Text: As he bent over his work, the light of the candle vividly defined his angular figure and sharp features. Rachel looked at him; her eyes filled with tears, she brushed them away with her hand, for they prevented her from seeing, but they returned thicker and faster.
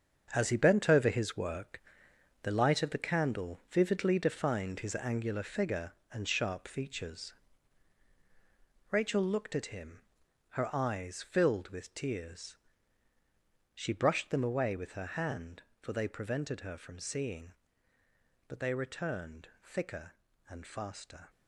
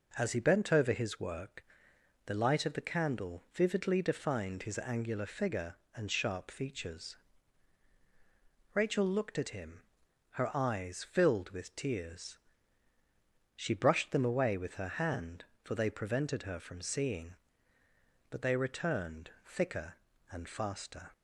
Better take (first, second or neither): second